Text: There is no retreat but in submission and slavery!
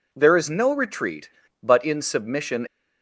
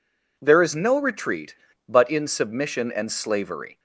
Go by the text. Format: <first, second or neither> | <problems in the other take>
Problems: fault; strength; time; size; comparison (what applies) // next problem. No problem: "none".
second | stops before "and slavery"; at 2.6 s